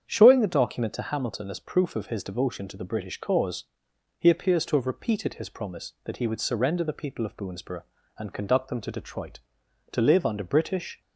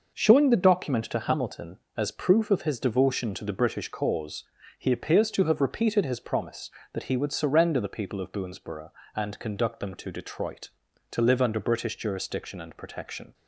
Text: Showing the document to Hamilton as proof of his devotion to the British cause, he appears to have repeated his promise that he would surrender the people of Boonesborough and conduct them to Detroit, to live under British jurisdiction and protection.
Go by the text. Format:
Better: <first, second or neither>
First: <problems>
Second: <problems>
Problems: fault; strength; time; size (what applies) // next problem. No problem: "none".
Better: second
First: starts louder than the rest; strong; until 1.0 s; 8 dB // stops before "jurisdiction and protection"; at 11.0 s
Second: none